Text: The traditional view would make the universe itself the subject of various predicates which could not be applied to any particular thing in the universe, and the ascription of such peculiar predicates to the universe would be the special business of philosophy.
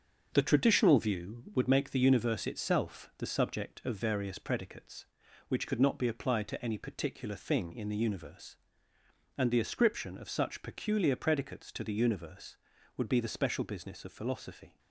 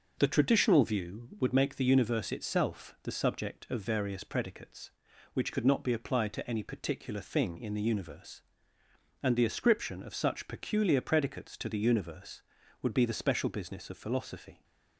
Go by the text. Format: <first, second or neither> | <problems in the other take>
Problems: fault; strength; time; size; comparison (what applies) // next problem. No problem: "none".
second | gets quieter; throughout; 6.5 dB // starts louder than the rest; until 1.3 s; 7 dB; noticeable in the second